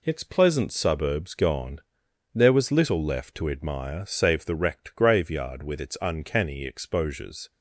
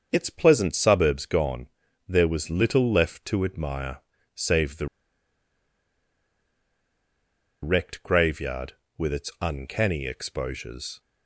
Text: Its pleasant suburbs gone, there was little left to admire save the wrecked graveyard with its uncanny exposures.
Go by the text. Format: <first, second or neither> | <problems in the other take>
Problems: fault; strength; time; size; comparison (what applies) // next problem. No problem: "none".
first | starts louder than the rest; until 1.1 s; 6.5 dB // pauses between "admire" and "save"; at 3.9 s; 0.38 s long // pauses between "the" and "wrecked"; strong; at 4.8 s; 2.7 s long